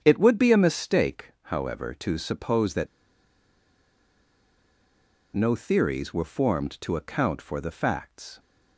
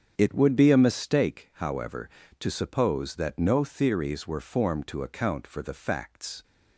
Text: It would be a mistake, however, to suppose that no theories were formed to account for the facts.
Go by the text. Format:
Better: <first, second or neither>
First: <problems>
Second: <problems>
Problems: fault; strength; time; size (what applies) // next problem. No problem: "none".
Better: second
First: starts louder than the rest; strong; until 1.0 s; 7.5 dB // pauses between "that" and "no"; strong; at 2.8 s; 2.4 s long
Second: starts louder than the rest; strong; until 1.2 s; 7.5 dB